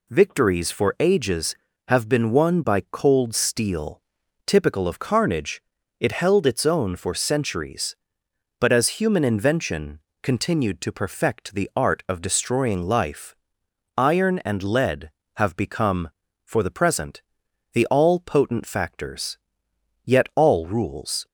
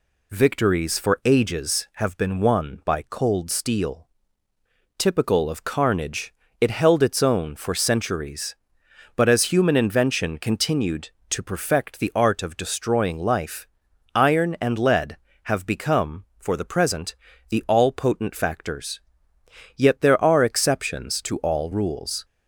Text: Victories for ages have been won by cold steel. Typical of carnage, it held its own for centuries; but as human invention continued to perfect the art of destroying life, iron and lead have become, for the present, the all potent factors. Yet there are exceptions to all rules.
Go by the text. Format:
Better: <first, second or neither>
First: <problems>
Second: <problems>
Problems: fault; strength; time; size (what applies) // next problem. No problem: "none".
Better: second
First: pauses between "invention" and "continued"; slight; at 9.9 s; 0.24 s long // skips "there are exceptions to"; at 20.3 s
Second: none